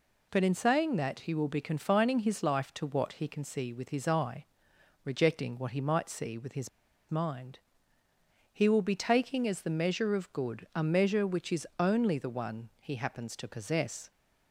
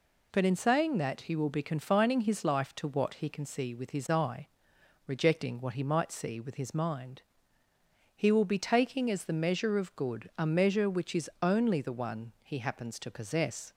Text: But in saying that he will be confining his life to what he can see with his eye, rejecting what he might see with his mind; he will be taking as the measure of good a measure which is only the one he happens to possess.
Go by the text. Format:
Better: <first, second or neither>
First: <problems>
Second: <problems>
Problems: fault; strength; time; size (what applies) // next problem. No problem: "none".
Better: second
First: pauses between "his" and "mind"; at 6.6 s; 0.40 s long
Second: none